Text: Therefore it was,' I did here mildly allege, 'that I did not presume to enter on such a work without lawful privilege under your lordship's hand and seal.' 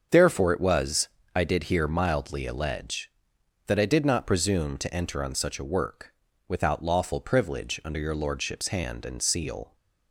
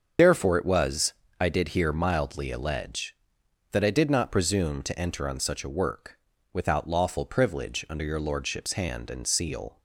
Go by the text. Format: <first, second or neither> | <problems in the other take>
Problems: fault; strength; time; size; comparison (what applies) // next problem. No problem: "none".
first | loses the start of "Therefore"; at 0.1 s; 35 ms // starts louder than the rest; until 1.4 s; 6.5 dB; also in the first // pauses between "work" and "without"; slight; at 6.1 s; 0.34 s long; slight in the first